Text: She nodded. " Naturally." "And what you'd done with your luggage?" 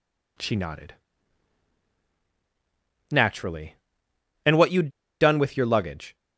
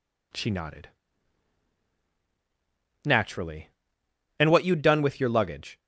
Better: second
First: pauses between "you'd" and "done"; slight; at 4.9 s; 0.30 s long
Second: none

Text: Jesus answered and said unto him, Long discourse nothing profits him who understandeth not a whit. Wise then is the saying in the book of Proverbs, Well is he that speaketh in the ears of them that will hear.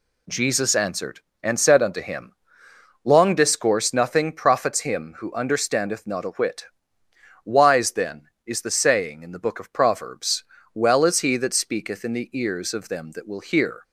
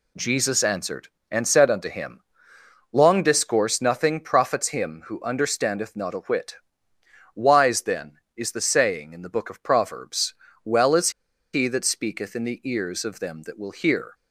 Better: first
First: none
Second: pauses between "is" and "he"; at 11.0 s; 0.43 s long

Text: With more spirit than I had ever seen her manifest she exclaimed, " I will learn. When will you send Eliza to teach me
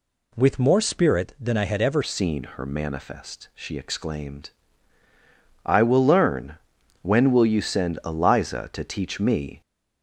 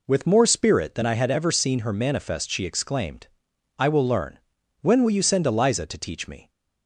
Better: second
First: changes voice at "seen"; from 2.0 s on; 7.6 s long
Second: none

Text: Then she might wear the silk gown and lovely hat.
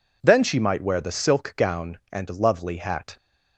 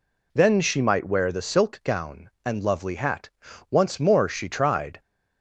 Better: first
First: none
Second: goes on to say "Once more she tried"; noticeable; from 3.7 s on; 1.2 s long

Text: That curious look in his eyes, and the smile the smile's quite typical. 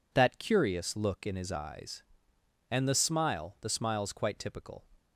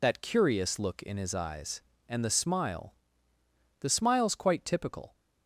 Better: first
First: none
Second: loses the start of "That"; at 0.0 s; 45 ms // pauses between "smile" and "the"; noticeable; at 2.9 s; 0.88 s long

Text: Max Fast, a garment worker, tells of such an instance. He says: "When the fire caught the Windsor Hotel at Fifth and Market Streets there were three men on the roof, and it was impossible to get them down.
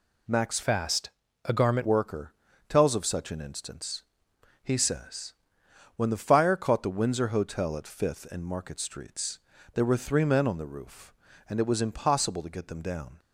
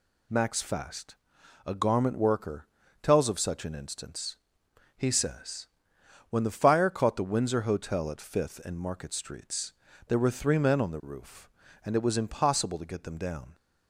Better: second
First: changes voice from "Fast" to "garment"; from 0.6 to 1.8 s; 1.2 s long // pauses between "Streets" and "there"; slight; at 9.3 s; 0.34 s long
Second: pauses between "Streets" and "there"; slight; at 9.7 s; 0.34 s long

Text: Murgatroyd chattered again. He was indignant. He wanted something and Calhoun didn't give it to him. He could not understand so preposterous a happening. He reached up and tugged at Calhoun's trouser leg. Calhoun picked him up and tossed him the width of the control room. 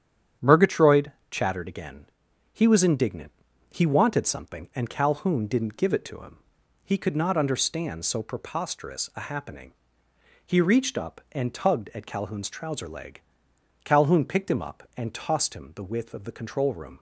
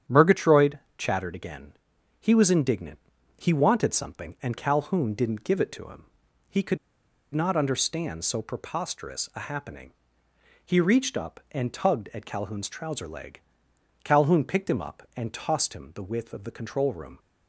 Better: first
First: starts louder than the rest; strong; until 1.6 s; 9 dB // pauses between "Murgatroyd" and "chattered"; slight; at 1.1 s; 0.18 s long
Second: starts louder than the rest; strong; until 1.2 s; 9 dB // pauses between "Murgatroyd" and "chattered"; slight; at 0.7 s; 0.18 s long // pauses between "could" and "not"; noticeable; at 6.7 s; 0.56 s long

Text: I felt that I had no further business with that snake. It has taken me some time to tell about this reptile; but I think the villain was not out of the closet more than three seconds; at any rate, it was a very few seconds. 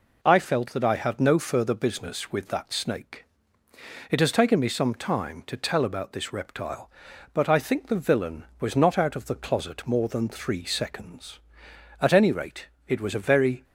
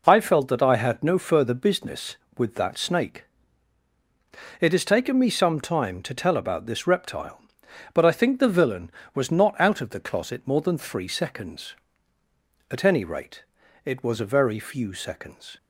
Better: second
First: stops before "few seconds"; at 13.6 s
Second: none

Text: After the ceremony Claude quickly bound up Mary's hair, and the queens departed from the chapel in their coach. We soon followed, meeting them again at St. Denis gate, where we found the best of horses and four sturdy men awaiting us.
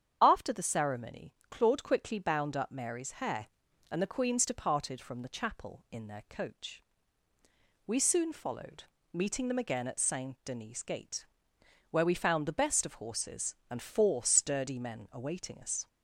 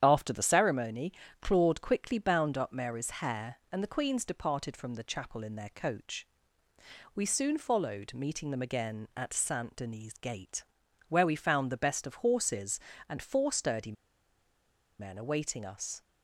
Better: first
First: starts louder than the rest; strong; until 1.2 s; 8 dB // pauses between "ceremony" and "Claude"; slight; at 1.3 s; 0.16 s long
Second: starts louder than the rest; strong; until 1.0 s; 9.5 dB // pauses between "ceremony" and "Claude"; slight; at 1.1 s; 0.28 s long // pauses between "sturdy" and "men"; at 13.9 s; 1.0 s long

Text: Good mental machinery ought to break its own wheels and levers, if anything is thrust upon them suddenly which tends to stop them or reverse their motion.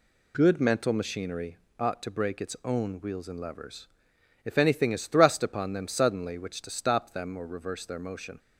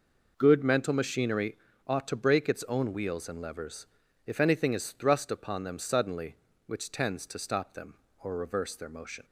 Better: second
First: pauses between "machinery" and "ought"; slight; at 1.5 s; 0.24 s long // skips "tends"; at 6.6 s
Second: pauses between "machinery" and "ought"; slight; at 1.5 s; 0.30 s long

